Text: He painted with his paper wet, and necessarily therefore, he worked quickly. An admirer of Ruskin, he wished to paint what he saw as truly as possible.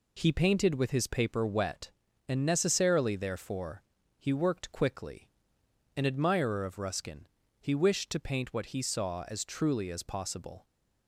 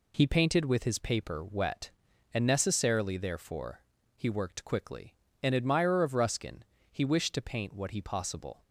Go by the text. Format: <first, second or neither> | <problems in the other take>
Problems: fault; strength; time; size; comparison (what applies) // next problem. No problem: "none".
first | skips "saw as truly as"; at 7.9 s